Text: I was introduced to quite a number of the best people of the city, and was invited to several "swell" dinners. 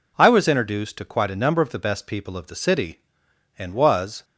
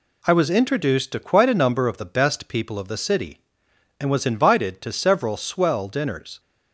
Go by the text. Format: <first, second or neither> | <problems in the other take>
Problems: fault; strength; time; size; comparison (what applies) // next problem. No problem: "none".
second | stops before "invited to several swell dinners"; at 4.2 s